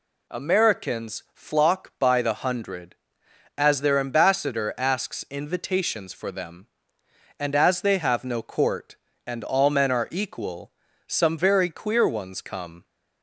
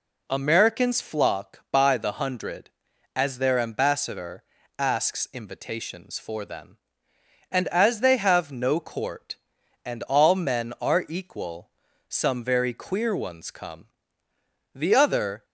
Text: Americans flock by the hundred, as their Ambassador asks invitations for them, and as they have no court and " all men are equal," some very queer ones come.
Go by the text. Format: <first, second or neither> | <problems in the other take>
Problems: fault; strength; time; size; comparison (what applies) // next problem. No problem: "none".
first | pauses between "Ambassador" and "asks"; slight; at 4.4 s; 0.34 s long // goes on to say "The other"; noticeable; from 14.7 s on; 0.70 s long